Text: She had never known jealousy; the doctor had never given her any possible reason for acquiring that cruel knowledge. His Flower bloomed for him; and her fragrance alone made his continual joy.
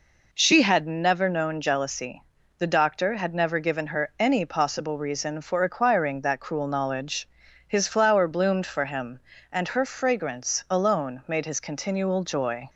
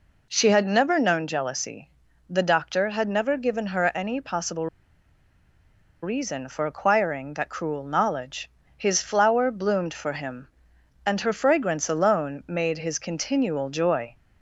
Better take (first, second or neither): first